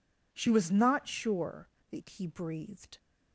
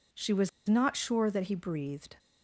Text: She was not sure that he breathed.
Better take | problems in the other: first | pauses between "was" and "not"; slight; at 0.4 s; 0.17 s long

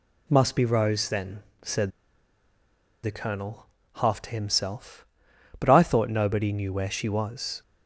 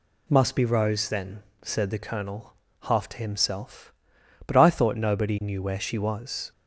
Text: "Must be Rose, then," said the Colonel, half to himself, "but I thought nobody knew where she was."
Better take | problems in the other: second | pauses between "said" and "the"; at 1.8 s; 1.1 s long

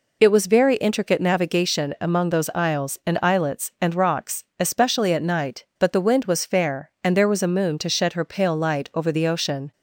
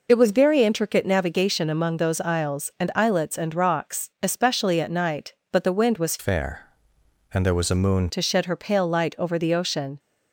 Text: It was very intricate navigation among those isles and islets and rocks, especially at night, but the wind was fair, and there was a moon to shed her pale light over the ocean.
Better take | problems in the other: first | changes voice from "fair" to "moon"; from 6.1 to 8.0 s; 1.9 s long

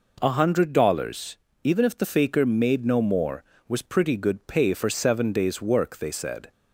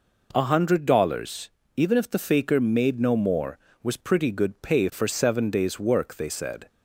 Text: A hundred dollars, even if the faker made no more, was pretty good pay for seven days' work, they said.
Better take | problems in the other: neither | none

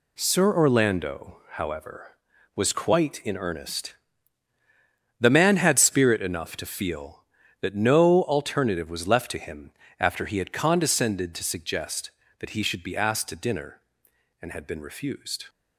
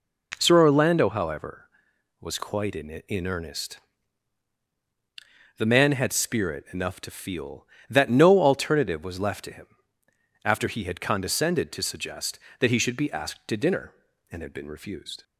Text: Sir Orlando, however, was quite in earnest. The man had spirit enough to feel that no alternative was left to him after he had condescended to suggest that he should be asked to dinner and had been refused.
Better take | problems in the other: first | says "in" twice; at 2.8 s // pauses between "him" and "after"; noticeable; at 9.6 s; 0.76 s long; slight in the first

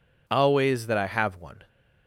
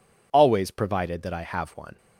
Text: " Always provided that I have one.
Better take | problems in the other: second | skips "provided"; at 0.8 s

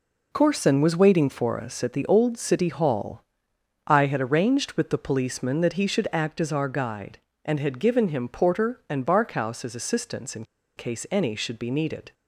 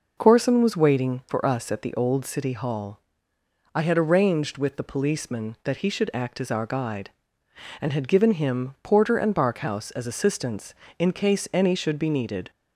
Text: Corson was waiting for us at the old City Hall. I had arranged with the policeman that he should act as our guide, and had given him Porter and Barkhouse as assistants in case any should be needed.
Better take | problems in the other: second | pauses between "in" and "case"; slight; at 10.4 s; 0.32 s long

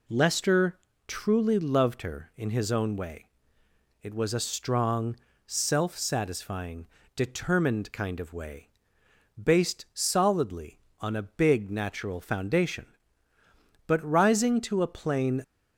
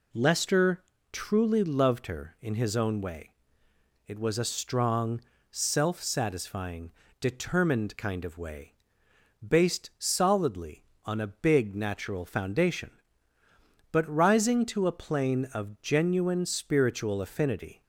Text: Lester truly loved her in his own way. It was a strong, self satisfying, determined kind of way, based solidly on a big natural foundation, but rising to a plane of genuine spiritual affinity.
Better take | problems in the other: second | pauses between "Lester" and "truly"; slight; at 0.7 s; 0.30 s long; slight in the second // stops before "of genuine spiritual affinity"; at 15.4 s

